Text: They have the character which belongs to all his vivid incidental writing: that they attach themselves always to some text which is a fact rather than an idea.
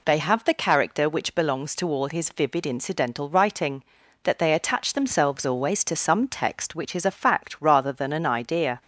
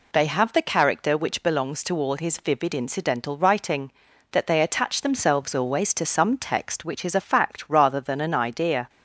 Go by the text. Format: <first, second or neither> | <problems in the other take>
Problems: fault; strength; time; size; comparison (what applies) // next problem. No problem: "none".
neither | none